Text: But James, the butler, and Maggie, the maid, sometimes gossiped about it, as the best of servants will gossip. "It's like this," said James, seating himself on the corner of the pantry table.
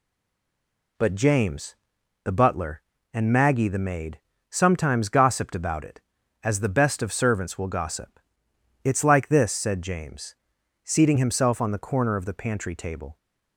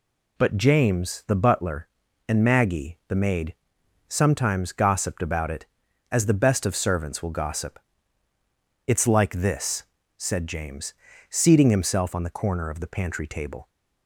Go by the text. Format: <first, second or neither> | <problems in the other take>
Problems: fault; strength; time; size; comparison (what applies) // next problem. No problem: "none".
second | stays silent before the first word; until 0.9 s; 0.9 s long